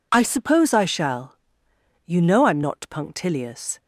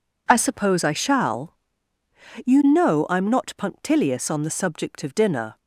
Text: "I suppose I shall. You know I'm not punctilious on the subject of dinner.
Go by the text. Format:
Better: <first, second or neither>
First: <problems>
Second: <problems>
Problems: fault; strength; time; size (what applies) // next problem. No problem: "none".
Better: second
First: stops before "on the subject of dinner"; at 3.7 s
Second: none